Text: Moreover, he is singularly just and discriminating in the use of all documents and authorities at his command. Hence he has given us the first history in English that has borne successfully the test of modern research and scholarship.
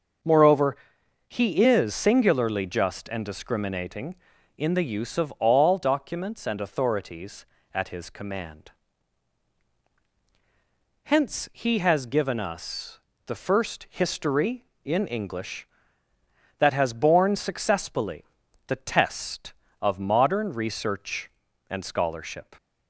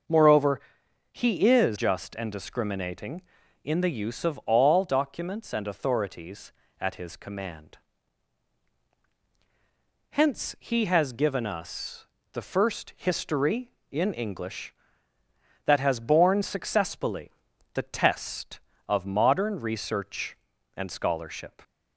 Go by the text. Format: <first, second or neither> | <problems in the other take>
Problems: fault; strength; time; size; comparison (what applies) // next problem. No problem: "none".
first | starts louder than the rest; noticeable; until 1.6 s; 6 dB; also in the first // skips "singularly"; at 1.7 s // pauses between "us" and "the"; slight; at 12.0 s; 0.26 s long; slight in the first // pauses between "successfully" and "the"; at 17.3 s; 0.42 s long; also in the first